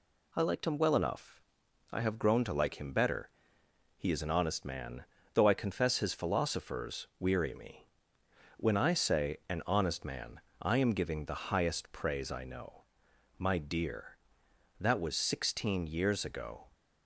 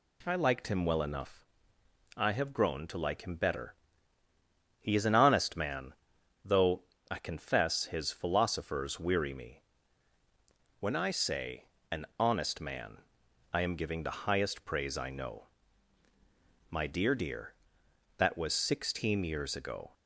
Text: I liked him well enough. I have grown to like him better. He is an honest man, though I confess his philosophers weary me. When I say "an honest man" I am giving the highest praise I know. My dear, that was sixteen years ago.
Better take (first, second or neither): first